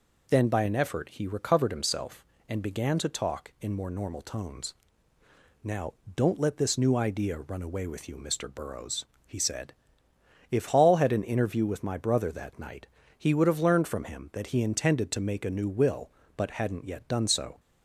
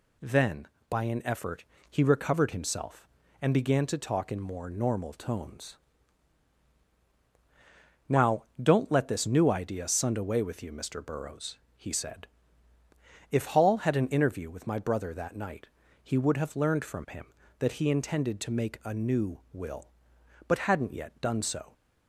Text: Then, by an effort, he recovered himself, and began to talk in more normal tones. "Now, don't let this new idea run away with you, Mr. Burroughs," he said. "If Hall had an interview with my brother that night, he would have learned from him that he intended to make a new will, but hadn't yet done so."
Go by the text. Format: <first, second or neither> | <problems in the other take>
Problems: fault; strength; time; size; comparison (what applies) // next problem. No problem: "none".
first | says "sund" for "run"; at 9.8 s